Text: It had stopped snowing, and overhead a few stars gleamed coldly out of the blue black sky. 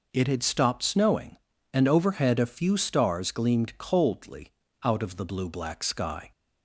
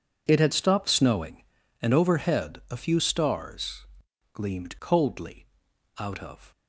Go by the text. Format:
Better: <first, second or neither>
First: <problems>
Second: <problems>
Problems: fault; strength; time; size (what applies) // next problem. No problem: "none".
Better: first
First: pauses between "coldly" and "out"; slight; at 4.4 s; 0.33 s long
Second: pauses between "stars" and "gleamed"; noticeable; at 3.8 s; 0.48 s long // pauses between "coldly" and "out"; noticeable; at 5.4 s; 0.54 s long // stops before "the blue black sky"; at 6.5 s